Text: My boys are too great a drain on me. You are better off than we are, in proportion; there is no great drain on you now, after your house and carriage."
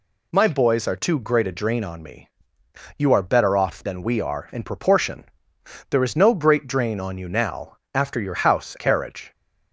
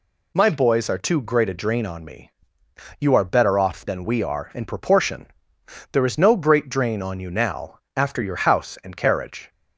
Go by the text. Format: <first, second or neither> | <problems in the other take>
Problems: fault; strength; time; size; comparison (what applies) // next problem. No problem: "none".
second | skips "and"; at 8.7 s